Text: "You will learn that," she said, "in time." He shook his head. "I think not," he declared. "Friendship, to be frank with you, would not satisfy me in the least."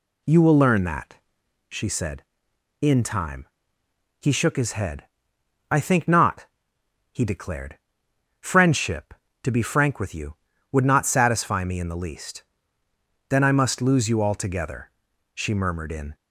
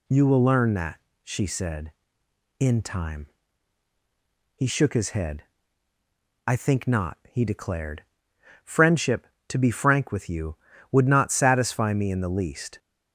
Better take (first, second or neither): second